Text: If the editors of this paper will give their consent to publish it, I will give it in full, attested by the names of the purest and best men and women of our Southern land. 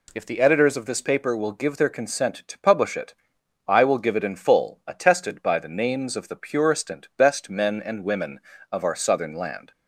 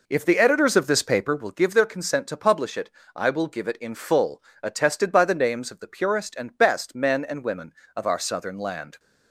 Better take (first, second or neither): first